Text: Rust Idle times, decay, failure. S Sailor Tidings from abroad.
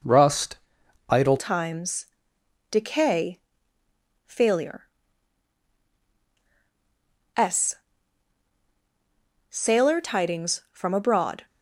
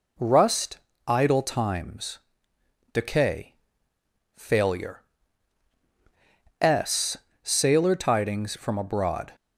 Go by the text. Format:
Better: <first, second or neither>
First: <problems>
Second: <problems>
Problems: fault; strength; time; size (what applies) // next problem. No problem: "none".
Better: second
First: pauses between "Rust" and "Idle"; noticeable; at 0.5 s; 0.52 s long // changes voice at "times"; from 1.3 s on; 10.1 s long // pauses between "S" and "Sailor"; strong; at 7.7 s; 1.7 s long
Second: pauses between "Rust" and "Idle"; slight; at 0.7 s; 0.28 s long // pauses between "S" and "Sailor"; slight; at 7.1 s; 0.24 s long